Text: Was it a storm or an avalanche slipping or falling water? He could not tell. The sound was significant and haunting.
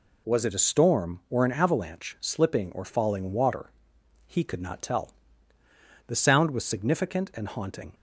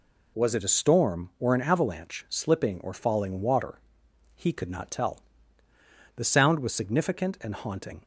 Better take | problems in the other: neither | none

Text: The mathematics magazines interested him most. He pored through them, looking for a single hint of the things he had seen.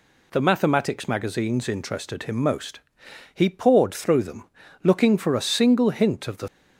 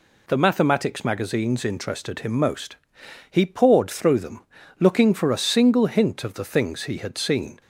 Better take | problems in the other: second | stops before "things he had seen"; at 6.4 s

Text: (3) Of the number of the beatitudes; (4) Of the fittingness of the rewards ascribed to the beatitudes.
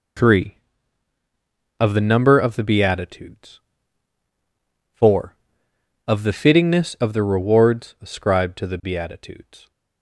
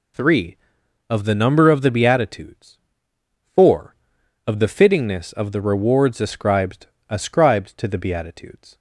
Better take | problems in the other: first | says "ascribed" twice; at 7.1 s

